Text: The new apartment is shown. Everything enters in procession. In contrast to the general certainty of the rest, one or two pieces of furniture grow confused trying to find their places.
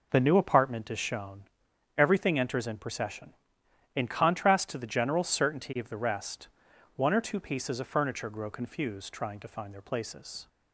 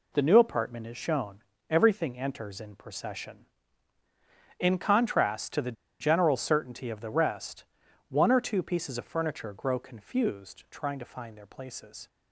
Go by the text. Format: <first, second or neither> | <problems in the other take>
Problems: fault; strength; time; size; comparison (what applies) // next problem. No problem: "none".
first | pauses between "the" and "general"; slight; at 5.7 s; 0.27 s long